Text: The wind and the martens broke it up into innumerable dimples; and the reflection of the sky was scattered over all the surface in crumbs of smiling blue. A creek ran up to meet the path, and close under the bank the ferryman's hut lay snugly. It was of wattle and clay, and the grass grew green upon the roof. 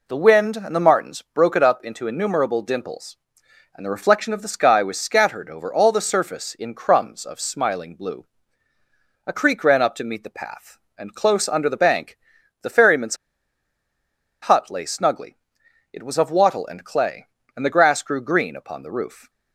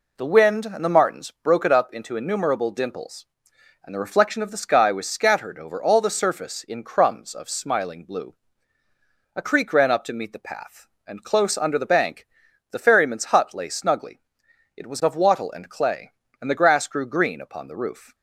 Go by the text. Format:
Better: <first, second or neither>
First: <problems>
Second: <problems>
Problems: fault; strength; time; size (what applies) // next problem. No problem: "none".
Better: second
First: pauses between "bank" and "the"; noticeable; at 12.1 s; 0.46 s long // pauses between "ferryman's" and "hut"; strong; at 13.1 s; 1.2 s long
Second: pauses between "bank" and "the"; noticeable; at 12.2 s; 0.46 s long